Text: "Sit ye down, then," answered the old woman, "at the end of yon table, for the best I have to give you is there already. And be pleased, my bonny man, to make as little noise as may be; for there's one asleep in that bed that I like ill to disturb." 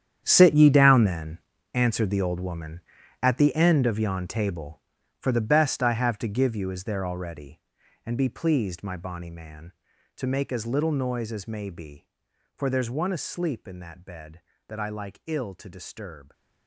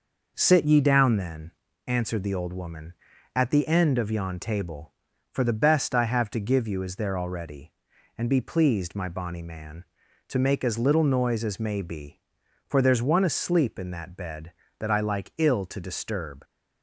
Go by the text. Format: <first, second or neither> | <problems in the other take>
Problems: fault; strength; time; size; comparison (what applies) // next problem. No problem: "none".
second | gets quieter; strong; throughout; 14.5 dB